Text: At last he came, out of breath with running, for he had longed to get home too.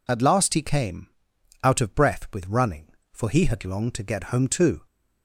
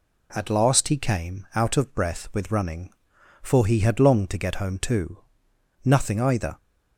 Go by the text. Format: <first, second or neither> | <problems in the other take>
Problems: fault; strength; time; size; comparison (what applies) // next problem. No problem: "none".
first | goes on to say "Nothing either"; noticeable; from 5.8 s on; 0.74 s long